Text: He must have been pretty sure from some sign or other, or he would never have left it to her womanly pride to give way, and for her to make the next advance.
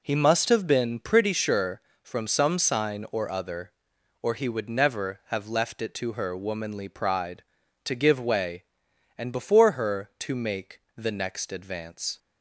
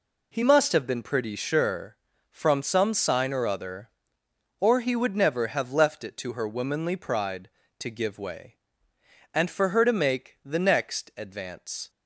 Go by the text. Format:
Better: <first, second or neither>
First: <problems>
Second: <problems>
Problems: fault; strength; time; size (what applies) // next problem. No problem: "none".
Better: second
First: says "before" for "for"; at 9.3 s // pauses between "make" and "the"; slight; at 10.8 s; 0.16 s long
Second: none